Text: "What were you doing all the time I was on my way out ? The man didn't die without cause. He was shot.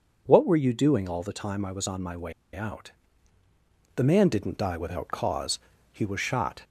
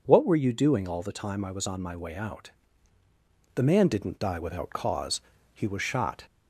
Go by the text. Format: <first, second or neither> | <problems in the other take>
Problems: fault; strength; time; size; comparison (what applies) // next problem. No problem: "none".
second | pauses between "way" and "out"; slight; at 2.3 s; 0.21 s long